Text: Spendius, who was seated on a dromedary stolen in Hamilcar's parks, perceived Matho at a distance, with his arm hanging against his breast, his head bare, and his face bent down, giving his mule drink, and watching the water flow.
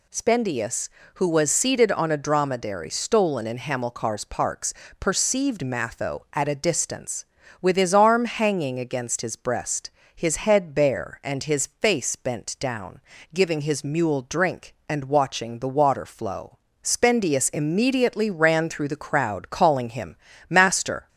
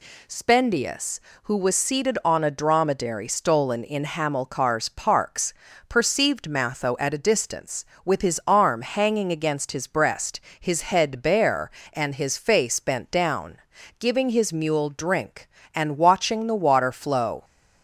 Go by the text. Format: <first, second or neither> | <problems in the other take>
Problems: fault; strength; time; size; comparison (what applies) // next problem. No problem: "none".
second | goes on to say "Spendius immediately ran through the crowd calling him Master"; strong; from 16.8 s on; 4.2 s long